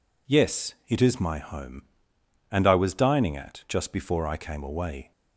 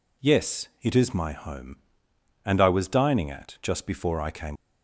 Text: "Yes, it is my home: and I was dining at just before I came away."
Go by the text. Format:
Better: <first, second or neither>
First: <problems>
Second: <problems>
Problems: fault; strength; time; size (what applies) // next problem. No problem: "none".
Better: first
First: none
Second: stops before "away"; at 4.5 s